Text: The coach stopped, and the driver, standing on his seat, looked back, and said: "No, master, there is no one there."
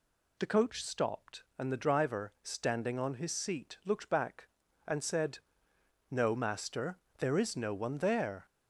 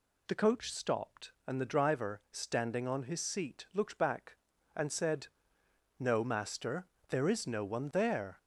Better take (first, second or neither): neither